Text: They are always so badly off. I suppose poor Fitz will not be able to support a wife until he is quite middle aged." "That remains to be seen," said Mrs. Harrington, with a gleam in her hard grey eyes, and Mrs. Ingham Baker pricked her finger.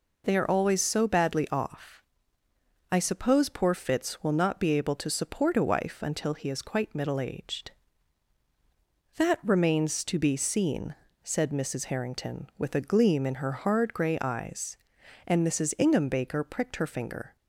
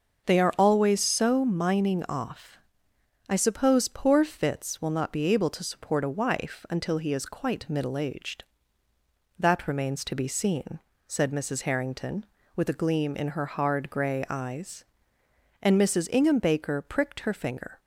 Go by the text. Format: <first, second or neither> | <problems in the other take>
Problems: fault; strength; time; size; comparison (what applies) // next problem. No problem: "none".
first | starts louder than the rest; until 1.3 s; 6.5 dB // says "mining" for "badly"; at 1.4 s